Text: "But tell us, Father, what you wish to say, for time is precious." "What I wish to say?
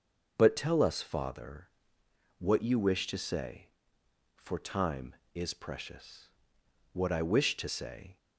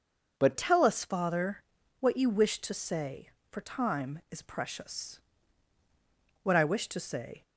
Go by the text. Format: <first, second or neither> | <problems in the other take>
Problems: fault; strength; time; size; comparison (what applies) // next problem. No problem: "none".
first | changes voice at "tell"; from 0.5 s on; 6.9 s long